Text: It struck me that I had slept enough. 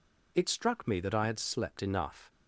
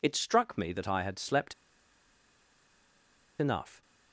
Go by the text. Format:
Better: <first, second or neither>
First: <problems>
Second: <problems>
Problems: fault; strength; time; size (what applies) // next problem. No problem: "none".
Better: first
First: none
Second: pauses between "slept" and "enough"; strong; at 1.5 s; 1.8 s long